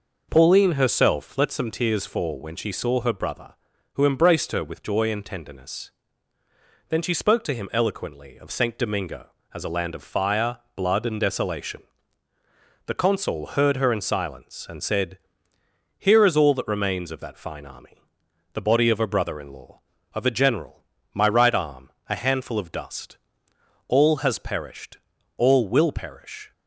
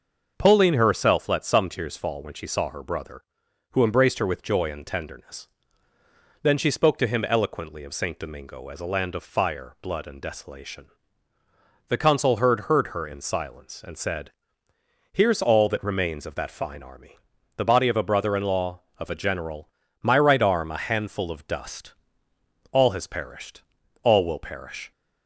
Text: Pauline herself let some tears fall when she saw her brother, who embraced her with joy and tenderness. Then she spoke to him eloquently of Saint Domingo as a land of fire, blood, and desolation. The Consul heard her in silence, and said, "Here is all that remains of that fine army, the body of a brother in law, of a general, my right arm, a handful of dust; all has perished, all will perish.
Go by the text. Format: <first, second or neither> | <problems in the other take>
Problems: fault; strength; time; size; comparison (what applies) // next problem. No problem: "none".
first | starts louder than the rest; until 1.3 s; 6.5 dB // says "heard" twice; at 12.6 s